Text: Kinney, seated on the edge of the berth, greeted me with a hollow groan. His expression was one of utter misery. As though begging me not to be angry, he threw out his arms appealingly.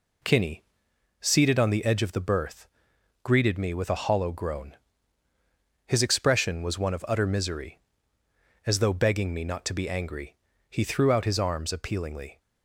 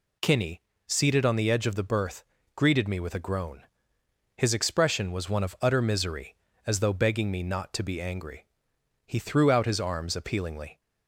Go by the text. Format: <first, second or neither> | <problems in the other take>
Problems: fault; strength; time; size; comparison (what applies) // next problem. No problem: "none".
first | skips "hollow"; at 3.1 s